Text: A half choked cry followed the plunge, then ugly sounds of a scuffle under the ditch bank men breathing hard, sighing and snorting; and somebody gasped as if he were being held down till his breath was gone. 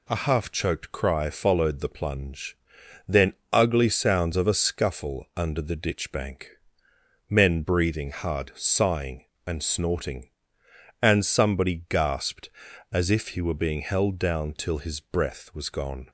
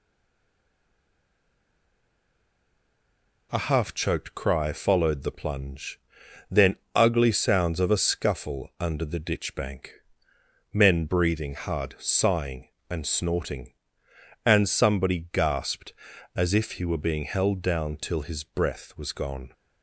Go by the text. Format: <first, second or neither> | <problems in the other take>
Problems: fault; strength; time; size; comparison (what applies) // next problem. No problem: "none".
first | stays silent before the first word; strong; until 3.5 s; 3.5 s long // pauses between "then" and "ugly"; slight; at 6.7 s; 0.20 s long; slight in the first // pauses between "bank" and "men"; noticeable; at 9.9 s; 0.76 s long; noticeable in the first